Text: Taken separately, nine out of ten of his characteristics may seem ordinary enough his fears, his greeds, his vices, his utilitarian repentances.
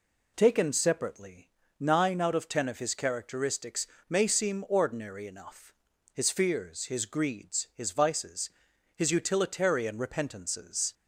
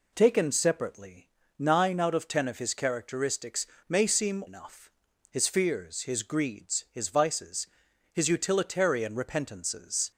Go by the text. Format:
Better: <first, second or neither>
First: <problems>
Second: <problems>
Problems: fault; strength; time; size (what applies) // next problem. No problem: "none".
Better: first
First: pauses between "characteristics" and "may"; slight; at 3.8 s; 0.24 s long // pauses between "enough" and "his"; at 5.6 s; 0.42 s long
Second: pauses between "characteristics" and "may"; slight; at 3.6 s; 0.24 s long // skips "ordinary"; at 4.4 s // pauses between "enough" and "his"; at 4.8 s; 0.42 s long